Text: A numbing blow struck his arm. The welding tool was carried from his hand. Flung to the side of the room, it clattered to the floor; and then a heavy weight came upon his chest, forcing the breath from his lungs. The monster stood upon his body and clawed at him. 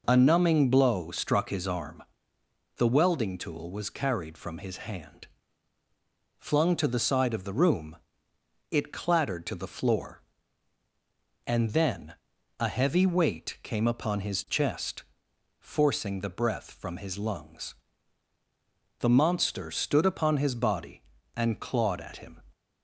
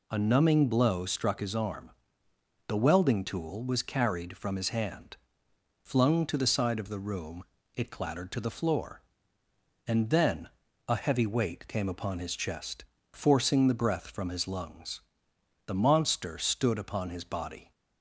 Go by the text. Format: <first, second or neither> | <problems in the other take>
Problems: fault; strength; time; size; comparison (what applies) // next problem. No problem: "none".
first | pauses between "then" and "a"; at 10.4 s; 0.38 s long; noticeable in the first // stops before "and clawed at him"; at 17.7 s